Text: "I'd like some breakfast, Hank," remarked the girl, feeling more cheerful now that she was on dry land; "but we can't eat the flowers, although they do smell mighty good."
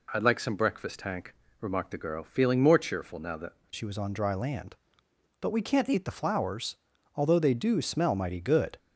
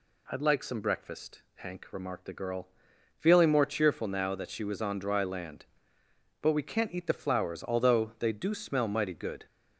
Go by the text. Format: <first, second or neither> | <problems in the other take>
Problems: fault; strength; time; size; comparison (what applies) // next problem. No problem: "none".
second | changes voice at "she"; from 3.7 s on; 5.0 s long